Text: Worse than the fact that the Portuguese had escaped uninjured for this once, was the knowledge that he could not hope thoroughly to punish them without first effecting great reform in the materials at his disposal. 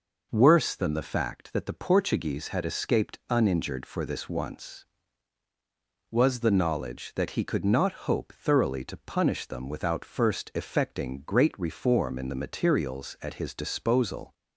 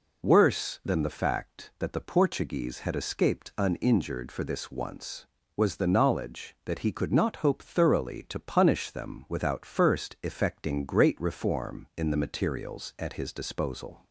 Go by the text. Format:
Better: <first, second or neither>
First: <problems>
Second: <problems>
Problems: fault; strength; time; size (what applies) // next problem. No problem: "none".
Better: neither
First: none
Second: none